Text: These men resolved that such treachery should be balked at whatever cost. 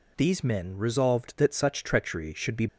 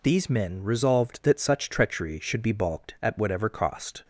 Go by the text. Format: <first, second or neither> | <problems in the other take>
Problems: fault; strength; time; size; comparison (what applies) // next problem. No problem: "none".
second | stops before "balked at whatever cost"; at 2.6 s